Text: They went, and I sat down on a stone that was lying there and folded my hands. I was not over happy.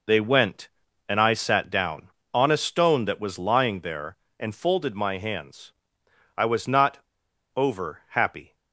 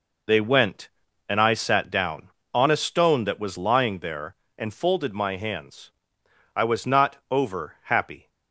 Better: second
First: pauses between "not" and "over"; noticeable; at 6.9 s; 0.56 s long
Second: none

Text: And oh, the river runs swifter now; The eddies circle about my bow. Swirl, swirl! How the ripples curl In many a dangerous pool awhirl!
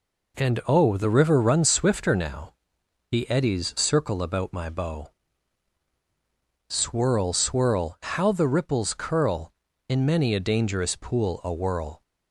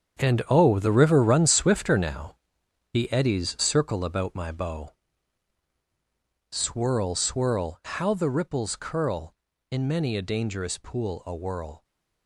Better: first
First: none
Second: gets quieter; strong; throughout; 11.5 dB

